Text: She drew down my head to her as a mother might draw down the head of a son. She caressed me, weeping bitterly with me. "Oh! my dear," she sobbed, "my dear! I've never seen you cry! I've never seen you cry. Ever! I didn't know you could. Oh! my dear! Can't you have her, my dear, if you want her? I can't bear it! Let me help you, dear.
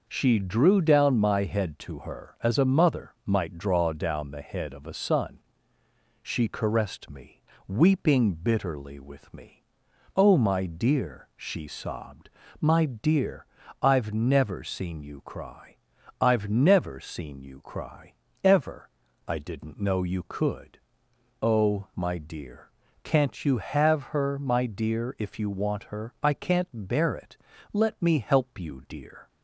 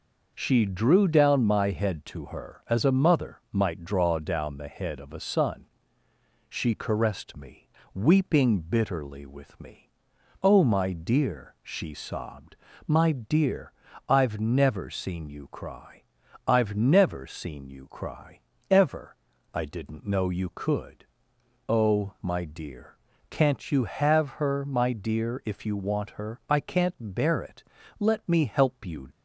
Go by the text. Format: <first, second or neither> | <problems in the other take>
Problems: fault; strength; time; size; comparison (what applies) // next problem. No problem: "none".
first | stops before "dear"; at 29.1 s